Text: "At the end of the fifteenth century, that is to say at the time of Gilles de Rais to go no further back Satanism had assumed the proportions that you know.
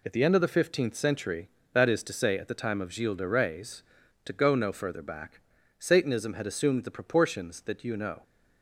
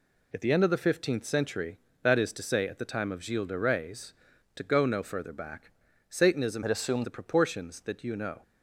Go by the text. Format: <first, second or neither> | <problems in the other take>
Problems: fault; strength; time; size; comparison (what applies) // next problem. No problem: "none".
first | pauses between "back" and "Satanism"; slight; at 5.7 s; 0.36 s long; slight in the first // changes voice from "had" to "assumed"; from 6.6 to 7.0 s; 0.4 s long